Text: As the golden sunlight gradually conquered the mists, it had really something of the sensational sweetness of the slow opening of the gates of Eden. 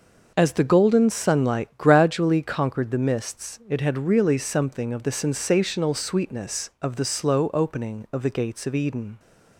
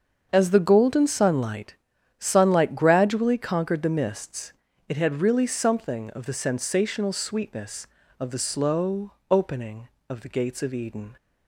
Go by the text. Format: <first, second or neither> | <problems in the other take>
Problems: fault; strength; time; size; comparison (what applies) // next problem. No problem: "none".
first | starts louder than the rest; until 1.3 s; 7 dB // says "sunlight" twice; at 2.1 s // pauses between "slow" and "opening"; slight; at 9.1 s; 0.18 s long